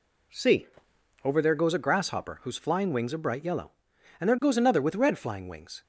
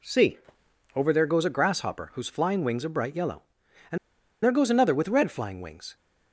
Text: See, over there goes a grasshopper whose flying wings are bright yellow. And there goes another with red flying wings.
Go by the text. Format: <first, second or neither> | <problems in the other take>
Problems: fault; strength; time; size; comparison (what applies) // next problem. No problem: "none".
first | pauses between "And" and "there"; noticeable; at 3.9 s; 0.47 s long